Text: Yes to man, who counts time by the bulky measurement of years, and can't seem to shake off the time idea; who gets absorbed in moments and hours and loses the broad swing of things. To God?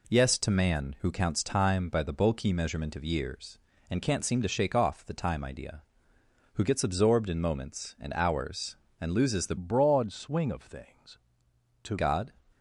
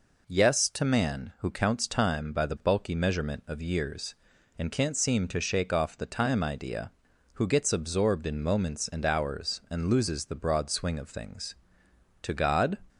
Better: second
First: changes voice from "broad" to "To"; from 9.5 to 11.9 s; 2.4 s long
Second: none

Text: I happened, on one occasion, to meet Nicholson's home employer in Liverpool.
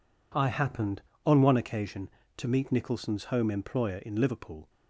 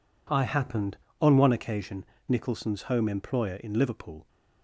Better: first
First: none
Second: skips "to meet"; at 2.1 s

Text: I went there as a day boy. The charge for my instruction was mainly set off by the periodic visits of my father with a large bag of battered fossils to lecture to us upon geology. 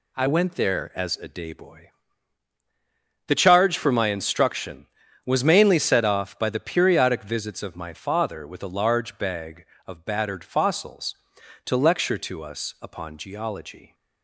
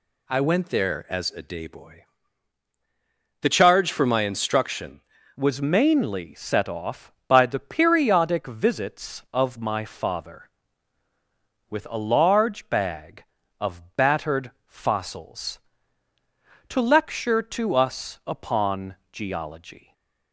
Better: first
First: none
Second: changes voice at "was"; from 5.3 s on; 14.6 s long // pauses between "of" and "battered"; slight; at 13.8 s; 0.16 s long // pauses between "upon" and "geology"; slight; at 18.9 s; 0.16 s long // stays silent after the last word; slight; from 19.7 s on; 0.6 s long

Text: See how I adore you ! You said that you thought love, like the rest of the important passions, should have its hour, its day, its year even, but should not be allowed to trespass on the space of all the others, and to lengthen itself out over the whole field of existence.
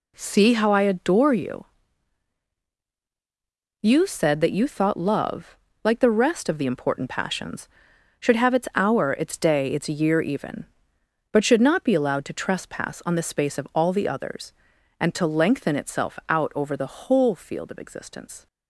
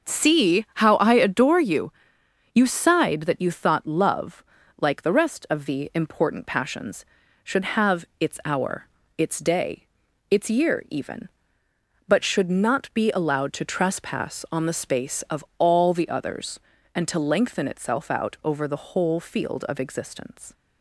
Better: first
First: none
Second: starts louder than the rest; until 1.1 s; 6 dB // says "sighed" for "said"; at 2.6 s

